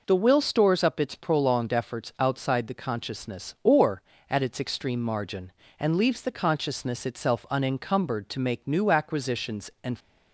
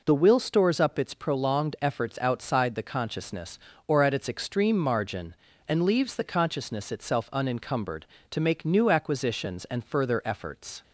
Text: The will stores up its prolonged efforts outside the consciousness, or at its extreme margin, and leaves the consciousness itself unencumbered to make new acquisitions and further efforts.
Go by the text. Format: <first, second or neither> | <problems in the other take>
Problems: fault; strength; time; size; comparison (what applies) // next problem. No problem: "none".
second | stops before "further efforts"; at 10.0 s